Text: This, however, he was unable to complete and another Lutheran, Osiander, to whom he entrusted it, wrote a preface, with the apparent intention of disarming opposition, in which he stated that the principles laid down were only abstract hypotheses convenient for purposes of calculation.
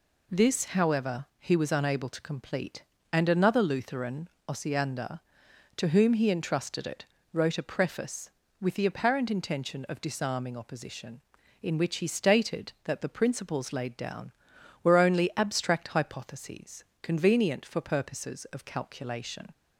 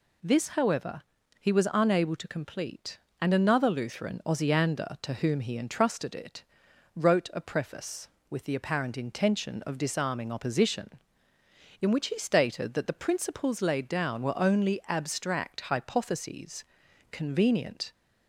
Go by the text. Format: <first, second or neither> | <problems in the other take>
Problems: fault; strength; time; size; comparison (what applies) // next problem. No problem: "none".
first | pauses between "hypotheses" and "convenient"; noticeable; at 16.6 s; 0.46 s long; slight in the first // stops before "for purposes of calculation"; at 17.9 s